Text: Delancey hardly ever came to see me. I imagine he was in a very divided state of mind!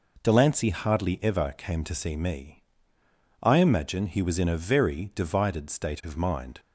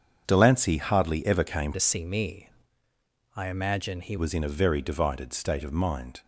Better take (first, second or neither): first